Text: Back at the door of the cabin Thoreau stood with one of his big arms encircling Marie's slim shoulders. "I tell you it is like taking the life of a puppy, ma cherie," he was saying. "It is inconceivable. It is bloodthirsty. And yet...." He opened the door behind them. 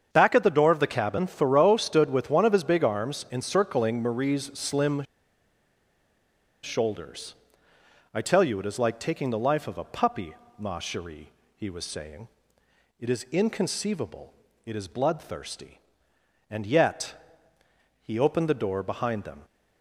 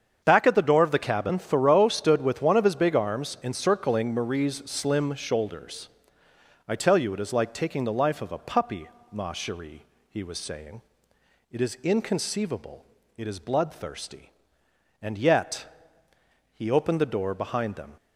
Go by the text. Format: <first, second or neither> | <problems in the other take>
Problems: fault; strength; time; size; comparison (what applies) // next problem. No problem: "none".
second | starts louder than the rest; strong; until 1.1 s; 7.5 dB; strong in the second // pauses between "slim" and "shoulders"; strong; at 5.0 s; 1.6 s long